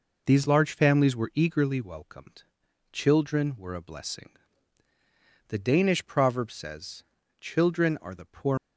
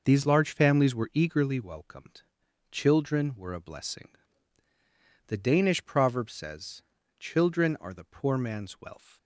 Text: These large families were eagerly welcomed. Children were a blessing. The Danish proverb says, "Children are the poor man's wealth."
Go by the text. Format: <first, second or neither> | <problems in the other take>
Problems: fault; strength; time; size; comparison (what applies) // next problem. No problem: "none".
second | stops before "man's wealth"; at 8.5 s